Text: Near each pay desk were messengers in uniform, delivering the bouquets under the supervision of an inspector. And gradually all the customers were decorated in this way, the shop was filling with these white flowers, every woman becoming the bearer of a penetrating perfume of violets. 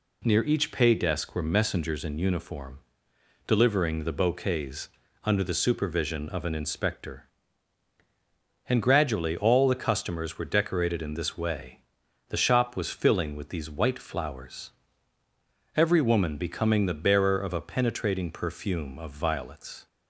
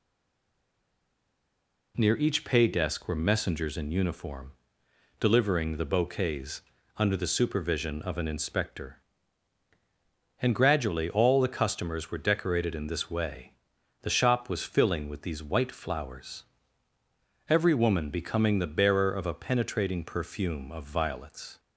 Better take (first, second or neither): first